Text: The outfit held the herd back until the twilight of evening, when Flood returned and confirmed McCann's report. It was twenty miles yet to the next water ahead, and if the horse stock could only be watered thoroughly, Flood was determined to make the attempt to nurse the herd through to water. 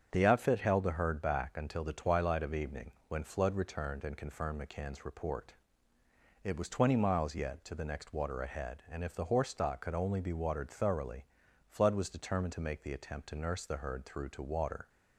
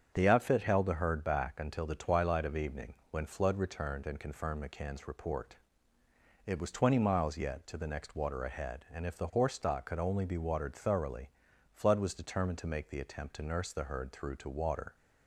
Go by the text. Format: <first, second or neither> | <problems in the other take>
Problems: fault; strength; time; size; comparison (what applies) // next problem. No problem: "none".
neither | starts louder than the rest; strong; the same in both